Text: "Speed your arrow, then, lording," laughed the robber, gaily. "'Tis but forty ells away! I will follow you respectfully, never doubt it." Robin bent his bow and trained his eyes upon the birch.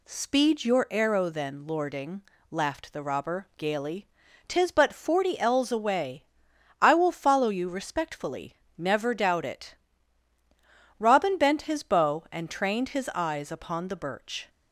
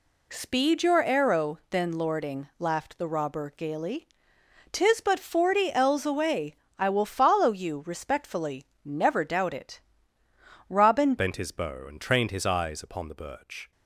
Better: first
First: none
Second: changes voice at "bent"; from 11.1 s on; 2.6 s long

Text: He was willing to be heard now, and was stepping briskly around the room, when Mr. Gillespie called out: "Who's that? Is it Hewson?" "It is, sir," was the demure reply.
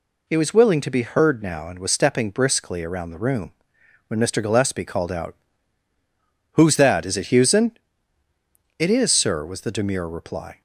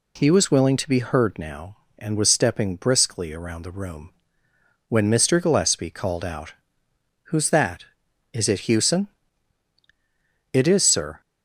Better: first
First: none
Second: stops before "was the demure reply"; at 11.2 s

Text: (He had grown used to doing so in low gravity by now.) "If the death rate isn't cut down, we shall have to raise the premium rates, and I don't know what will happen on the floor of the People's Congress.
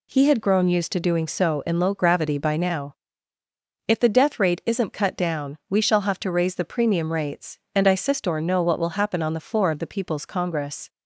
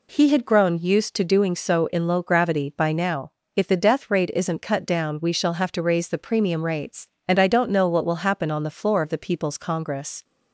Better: second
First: says "sistor" for "don't"; at 7.9 s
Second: none

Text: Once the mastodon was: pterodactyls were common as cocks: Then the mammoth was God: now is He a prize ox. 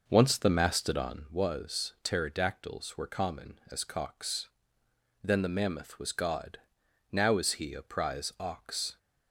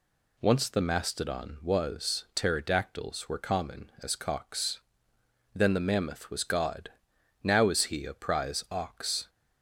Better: second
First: starts louder than the rest; noticeable; until 1.2 s; 5.5 dB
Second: none

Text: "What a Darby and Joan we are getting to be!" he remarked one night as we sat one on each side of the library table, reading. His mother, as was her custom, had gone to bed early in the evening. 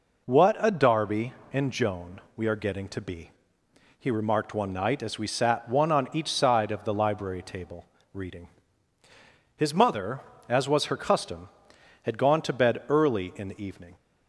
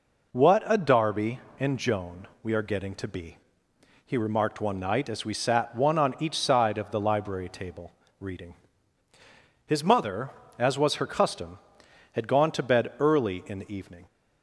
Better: neither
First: pauses between "Joan" and "we"; slight; at 2.1 s; 0.16 s long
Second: pauses between "Joan" and "we"; slight; at 2.2 s; 0.16 s long

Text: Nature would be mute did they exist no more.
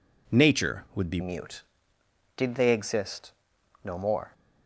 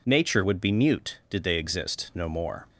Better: second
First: changes voice at "mute"; from 1.1 s on; 3.2 s long // pauses between "exist" and "no"; noticeable; at 3.3 s; 0.52 s long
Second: none

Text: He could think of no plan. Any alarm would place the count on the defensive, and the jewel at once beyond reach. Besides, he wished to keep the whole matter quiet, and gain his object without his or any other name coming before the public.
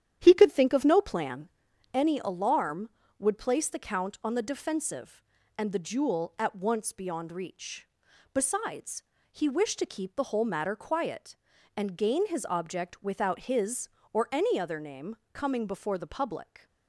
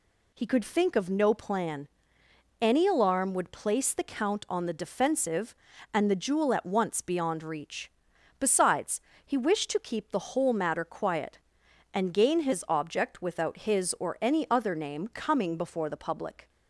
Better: second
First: starts louder than the rest; strong; until 1.5 s; 10.5 dB // pauses between "name" and "coming"; slight; at 15.1 s; 0.18 s long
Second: none

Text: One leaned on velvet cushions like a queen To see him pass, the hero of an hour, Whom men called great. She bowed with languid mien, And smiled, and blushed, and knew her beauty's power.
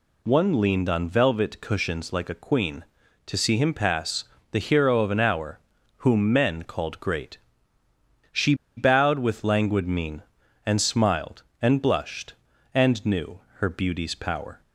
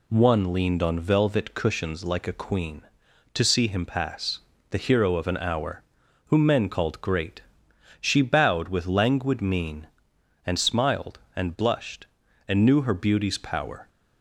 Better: second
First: pauses between "She" and "bowed"; slight; at 8.5 s; 0.22 s long // pauses between "knew" and "her"; slight; at 13.3 s; 0.16 s long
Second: none

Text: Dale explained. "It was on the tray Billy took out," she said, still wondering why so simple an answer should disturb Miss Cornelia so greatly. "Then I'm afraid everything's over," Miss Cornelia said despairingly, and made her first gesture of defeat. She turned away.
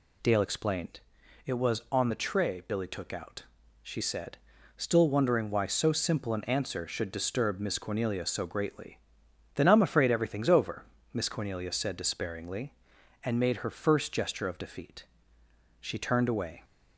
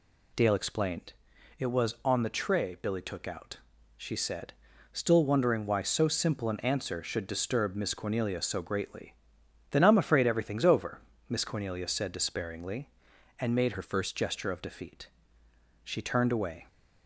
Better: first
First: none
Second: changes voice from "her" to "first"; from 13.7 to 14.1 s; 0.4 s long

